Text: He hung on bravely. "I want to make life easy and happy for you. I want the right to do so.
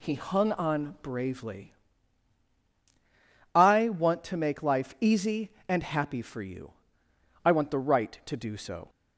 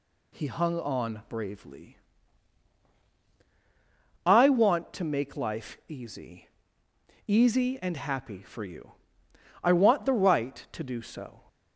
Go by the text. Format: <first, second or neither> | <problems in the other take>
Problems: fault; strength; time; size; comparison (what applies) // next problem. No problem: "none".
first | says "easy" twice; at 7.2 s